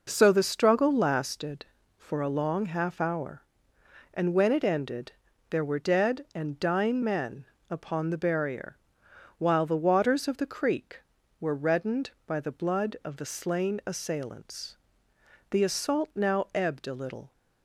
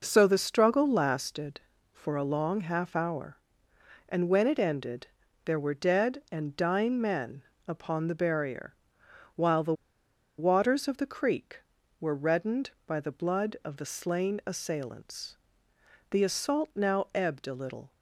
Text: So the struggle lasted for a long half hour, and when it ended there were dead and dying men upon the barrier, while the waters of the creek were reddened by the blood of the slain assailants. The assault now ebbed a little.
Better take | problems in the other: first | pauses between "ended" and "there"; at 5.0 s; 0.38 s long; also in the first // pauses between "men" and "upon"; slight; at 7.4 s; 0.28 s long; slight in the first // pauses between "the" and "waters"; noticeable; at 9.7 s; 0.65 s long

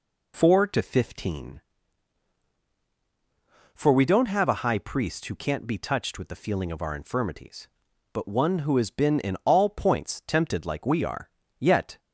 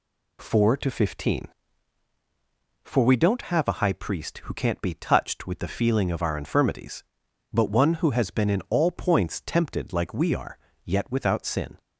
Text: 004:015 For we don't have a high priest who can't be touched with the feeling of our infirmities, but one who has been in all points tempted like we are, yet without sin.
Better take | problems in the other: second | stops before "without sin"; at 11.9 s

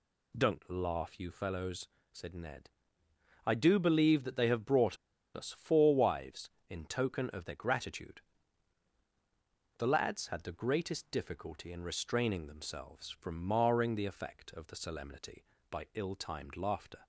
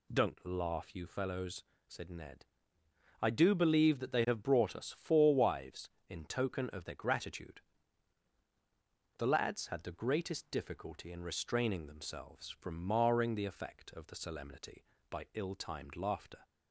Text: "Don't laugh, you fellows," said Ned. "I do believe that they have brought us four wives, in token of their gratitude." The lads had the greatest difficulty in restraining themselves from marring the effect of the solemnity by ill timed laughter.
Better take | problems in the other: second | pauses between "brought" and "us"; at 4.9 s; 0.37 s long

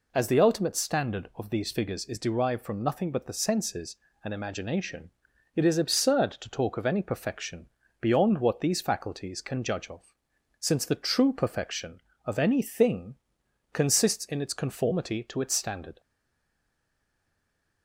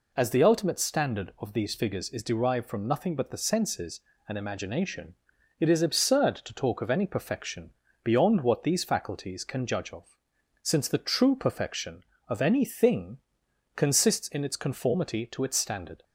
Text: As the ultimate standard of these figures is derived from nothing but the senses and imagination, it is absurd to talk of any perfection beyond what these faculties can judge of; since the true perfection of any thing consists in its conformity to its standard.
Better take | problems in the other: second | pauses between "perfection" and "beyond"; slight; at 7.6 s; 0.34 s long; slight in the second // pauses between "thing" and "consists"; noticeable; at 13.1 s; 0.58 s long; noticeable in the second // stays silent after the last word; noticeable; from 15.9 s on; 1.9 s long

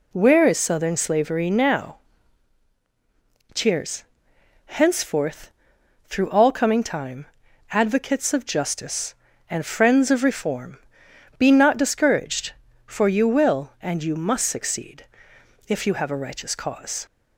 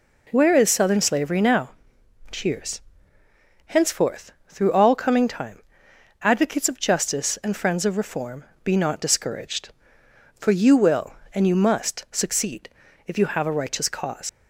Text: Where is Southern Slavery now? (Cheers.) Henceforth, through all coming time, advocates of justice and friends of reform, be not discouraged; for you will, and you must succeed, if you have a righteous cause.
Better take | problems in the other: first | leaves "cause" unfinished; at 14.2 s; 100 ms

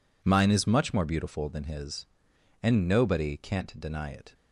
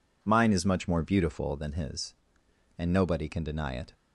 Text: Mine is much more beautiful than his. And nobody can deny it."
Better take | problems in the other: second | says "can't" for "can"; at 3.3 s

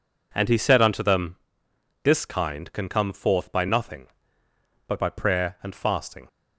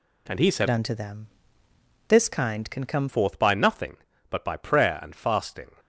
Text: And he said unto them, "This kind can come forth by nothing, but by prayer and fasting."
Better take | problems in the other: first | changes voice from "unto" to "come"; from 0.6 to 3.0 s; 2.4 s long

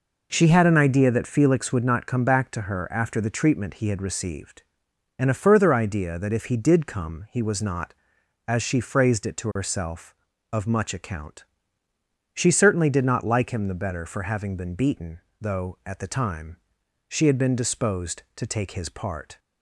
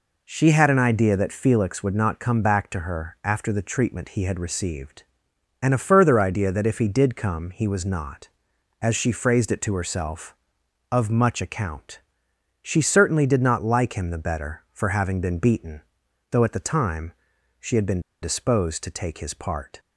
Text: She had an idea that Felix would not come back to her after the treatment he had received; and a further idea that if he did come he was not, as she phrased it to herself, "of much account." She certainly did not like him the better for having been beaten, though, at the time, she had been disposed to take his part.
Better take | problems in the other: first | pauses between "been" and "disposed"; slight; at 17.9 s; 0.23 s long

